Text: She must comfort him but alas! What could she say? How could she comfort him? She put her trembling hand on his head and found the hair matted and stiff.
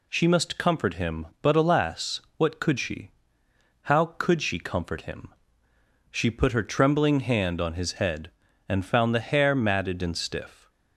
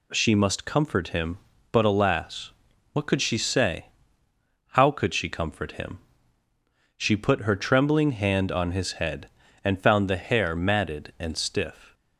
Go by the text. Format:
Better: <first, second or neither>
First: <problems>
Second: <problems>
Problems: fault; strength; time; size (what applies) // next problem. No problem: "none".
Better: second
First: skips "say"; at 3.4 s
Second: none